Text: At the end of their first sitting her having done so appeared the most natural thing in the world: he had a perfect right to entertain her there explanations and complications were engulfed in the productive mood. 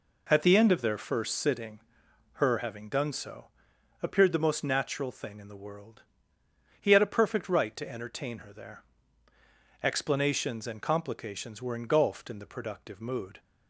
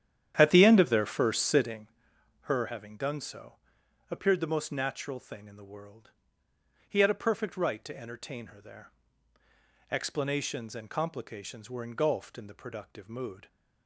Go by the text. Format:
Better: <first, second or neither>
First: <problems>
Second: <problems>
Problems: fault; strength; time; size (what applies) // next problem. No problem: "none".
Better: first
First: pauses between "sitting" and "her"; noticeable; at 1.7 s; 0.54 s long // pauses between "so" and "appeared"; noticeable; at 3.4 s; 0.56 s long // pauses between "there" and "explanations"; noticeable; at 8.8 s; 0.98 s long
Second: starts louder than the rest; strong; until 1.9 s; 10 dB // pauses between "sitting" and "her"; noticeable; at 1.8 s; 0.54 s long // pauses between "so" and "appeared"; noticeable; at 3.5 s; 0.56 s long // pauses between "there" and "explanations"; noticeable; at 8.9 s; 0.98 s long